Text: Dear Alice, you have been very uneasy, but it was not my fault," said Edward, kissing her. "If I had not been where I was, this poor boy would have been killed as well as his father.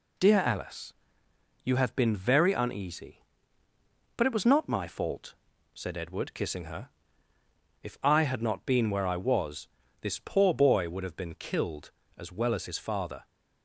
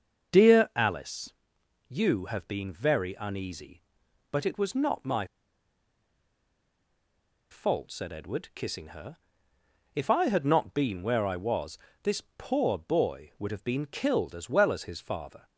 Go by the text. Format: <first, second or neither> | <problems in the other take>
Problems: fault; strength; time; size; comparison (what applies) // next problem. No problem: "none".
first | starts louder than the rest; until 1.9 s; 6.5 dB // pauses between "my" and "fault"; strong; at 5.2 s; 2.2 s long // pauses between "this" and "poor"; slight; at 12.2 s; 0.16 s long